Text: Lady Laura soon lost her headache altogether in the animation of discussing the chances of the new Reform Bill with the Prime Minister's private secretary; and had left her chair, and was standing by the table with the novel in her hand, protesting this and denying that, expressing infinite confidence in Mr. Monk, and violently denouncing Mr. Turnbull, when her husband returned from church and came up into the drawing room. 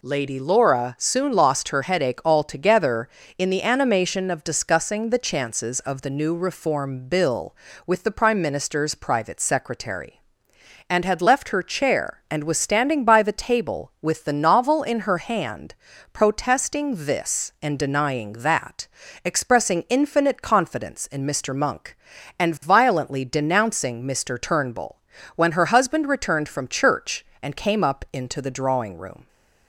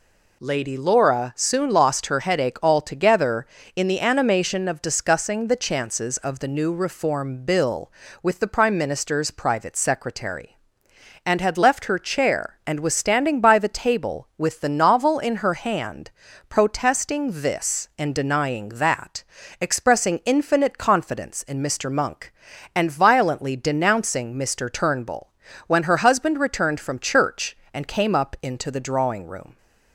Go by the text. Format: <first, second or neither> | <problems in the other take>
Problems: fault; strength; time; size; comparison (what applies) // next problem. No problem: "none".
neither | none